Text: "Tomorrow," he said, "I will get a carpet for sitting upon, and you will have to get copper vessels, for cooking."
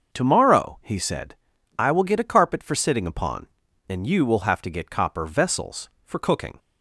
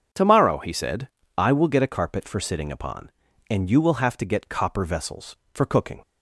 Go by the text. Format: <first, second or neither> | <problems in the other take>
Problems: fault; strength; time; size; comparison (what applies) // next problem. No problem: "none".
neither | starts louder than the rest; the same in both